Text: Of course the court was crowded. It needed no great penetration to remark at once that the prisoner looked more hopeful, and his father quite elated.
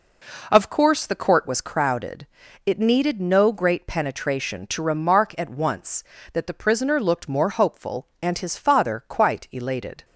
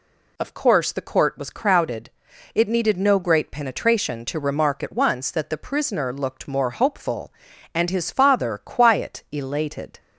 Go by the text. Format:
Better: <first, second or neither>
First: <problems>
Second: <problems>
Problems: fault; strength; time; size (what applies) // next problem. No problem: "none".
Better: first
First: none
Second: says "quiet" for "quite"; at 8.5 s